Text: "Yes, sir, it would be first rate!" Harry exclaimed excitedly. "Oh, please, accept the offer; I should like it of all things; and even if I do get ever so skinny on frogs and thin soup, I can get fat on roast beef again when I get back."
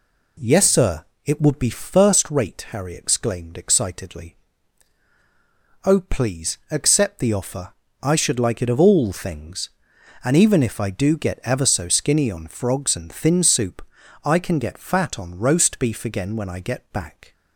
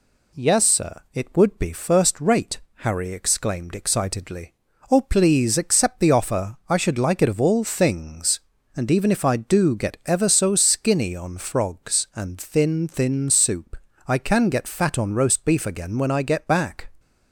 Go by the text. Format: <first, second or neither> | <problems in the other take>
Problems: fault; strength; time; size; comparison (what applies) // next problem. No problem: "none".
first | says "thin" twice; at 12.8 s